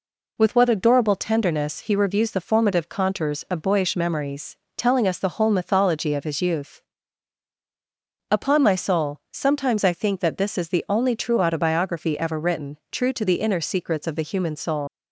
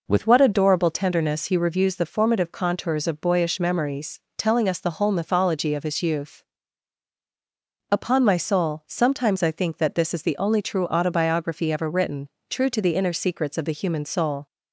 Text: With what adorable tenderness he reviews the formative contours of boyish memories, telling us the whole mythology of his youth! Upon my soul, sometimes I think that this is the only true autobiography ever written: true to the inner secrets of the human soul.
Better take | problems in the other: second | leaves "soul" unfinished; at 14.8 s; 95 ms

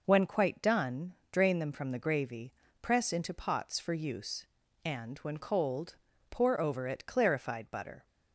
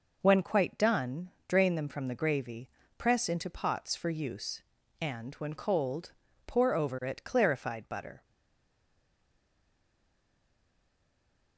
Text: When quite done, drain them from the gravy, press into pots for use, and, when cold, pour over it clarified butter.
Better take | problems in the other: first | stays silent after the last word; strong; from 8.2 s on; 3.3 s long

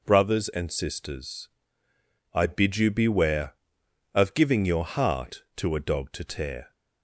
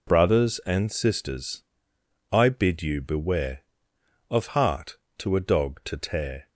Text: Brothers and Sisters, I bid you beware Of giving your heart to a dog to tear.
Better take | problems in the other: first | skips "giving your"; at 4.4 s

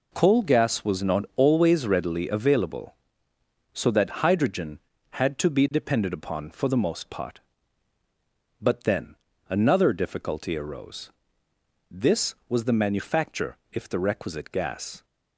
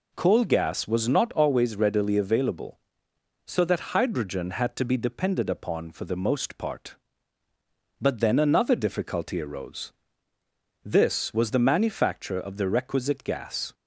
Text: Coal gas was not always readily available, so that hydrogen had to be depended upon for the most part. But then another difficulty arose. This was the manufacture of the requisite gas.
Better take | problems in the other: second | pauses between "then" and "another"; slight; at 9.1 s; 0.32 s long // says "if" for "of"; at 13.7 s

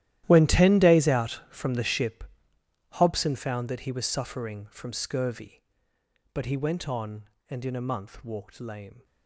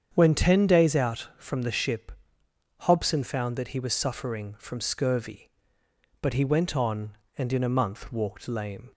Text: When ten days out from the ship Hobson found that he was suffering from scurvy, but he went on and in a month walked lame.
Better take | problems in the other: second | gets quieter; strong; throughout; 18.5 dB // starts louder than the rest; strong; until 1.2 s; 13.5 dB; strong in the second // pauses between "ship" and "Hobson"; noticeable; at 2.2 s; 0.68 s long; noticeable in the second

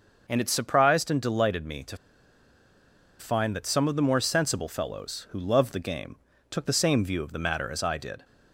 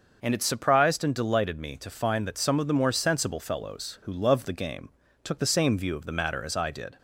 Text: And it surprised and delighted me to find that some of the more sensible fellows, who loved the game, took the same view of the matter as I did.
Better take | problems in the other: second | starts louder than the rest; noticeable; until 1.2 s; 6 dB; noticeable in the second // pauses between "to" and "find"; at 1.9 s; 1.2 s long

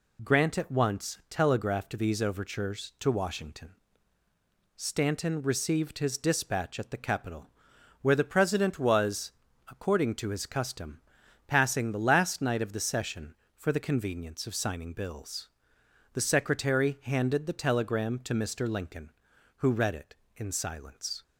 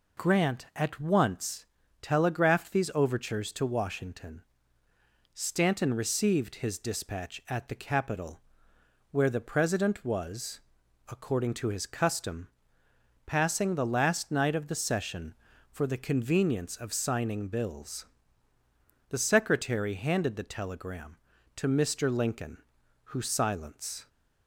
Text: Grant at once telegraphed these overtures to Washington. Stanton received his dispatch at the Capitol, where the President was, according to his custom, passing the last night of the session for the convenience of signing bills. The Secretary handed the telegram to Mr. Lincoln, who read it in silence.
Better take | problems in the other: first | pauses between "once" and "telegraphed"; at 1.6 s; 0.38 s long // skips "read it in"; at 23.2 s

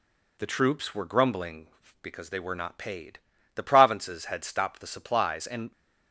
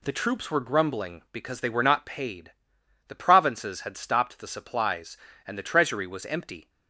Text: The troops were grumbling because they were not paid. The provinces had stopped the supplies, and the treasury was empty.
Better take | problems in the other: second | stops before "the treasury was empty"; at 5.7 s

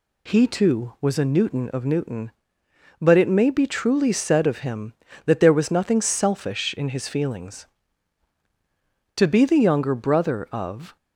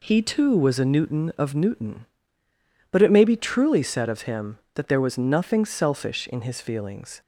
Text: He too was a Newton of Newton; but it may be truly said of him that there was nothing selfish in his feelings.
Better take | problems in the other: second | goes on to say "To be the younger brother of"; strong; from 9.1 s on; 1.8 s long

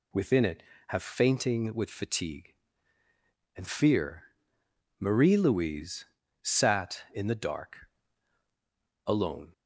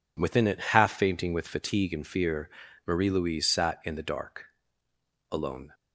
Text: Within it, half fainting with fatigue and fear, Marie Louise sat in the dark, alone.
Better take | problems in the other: second | says "have" for "half"; at 0.8 s // pauses between "Louise" and "sat"; at 6.0 s; 0.38 s long

